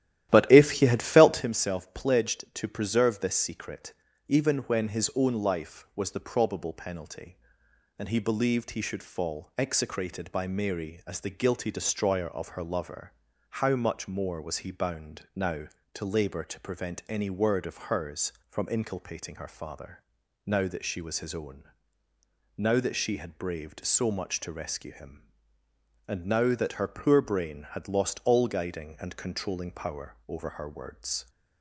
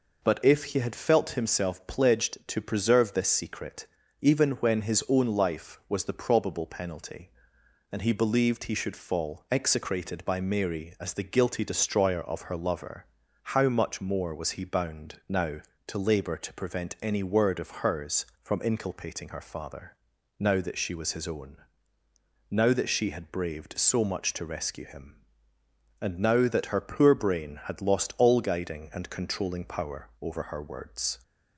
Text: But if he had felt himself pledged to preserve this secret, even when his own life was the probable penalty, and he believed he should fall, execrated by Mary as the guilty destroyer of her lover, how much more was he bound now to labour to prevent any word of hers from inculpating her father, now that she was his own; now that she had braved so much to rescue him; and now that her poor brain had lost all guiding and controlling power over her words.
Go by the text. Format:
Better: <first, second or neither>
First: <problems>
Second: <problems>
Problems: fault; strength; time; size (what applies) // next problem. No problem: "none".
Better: second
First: starts louder than the rest; strong; until 1.5 s; 13 dB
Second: none